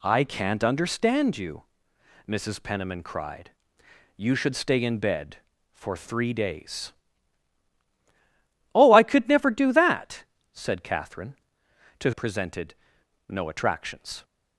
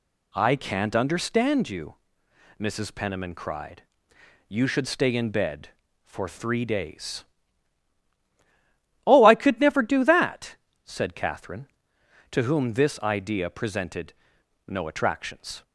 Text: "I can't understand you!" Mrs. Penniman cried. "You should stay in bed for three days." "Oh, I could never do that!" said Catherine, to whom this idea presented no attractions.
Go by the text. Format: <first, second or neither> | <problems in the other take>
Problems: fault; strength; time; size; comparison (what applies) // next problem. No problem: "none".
second | skips "whom this idea"; at 12.1 s // pauses between "presented" and "no"; noticeable; at 12.7 s; 0.56 s long; noticeable in the second